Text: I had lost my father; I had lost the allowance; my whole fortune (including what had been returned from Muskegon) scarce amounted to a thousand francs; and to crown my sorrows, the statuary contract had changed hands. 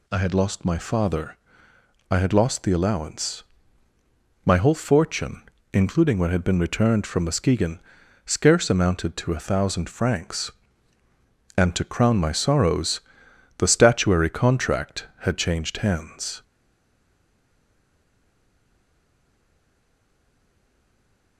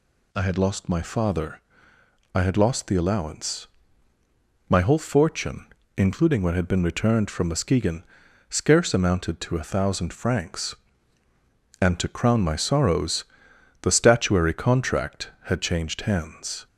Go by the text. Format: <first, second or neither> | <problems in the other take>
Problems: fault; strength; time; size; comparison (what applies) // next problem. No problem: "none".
second | stays silent after the last word; strong; from 16.4 s on; 4.9 s long